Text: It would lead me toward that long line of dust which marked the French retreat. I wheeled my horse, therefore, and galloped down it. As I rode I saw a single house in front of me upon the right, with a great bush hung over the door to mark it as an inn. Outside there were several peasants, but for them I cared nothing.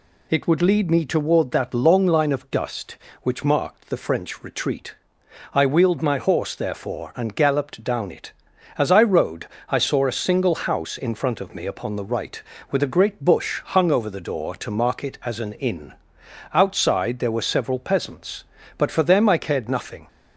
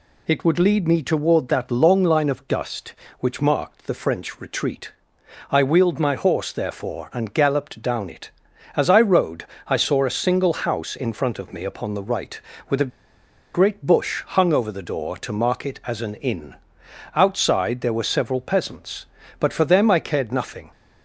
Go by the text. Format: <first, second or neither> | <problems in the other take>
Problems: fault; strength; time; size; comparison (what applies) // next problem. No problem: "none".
first | pauses between "rode" and "I"; slight; at 9.4 s; 0.22 s long; slight in the first // pauses between "a" and "great"; noticeable; at 12.9 s; 0.64 s long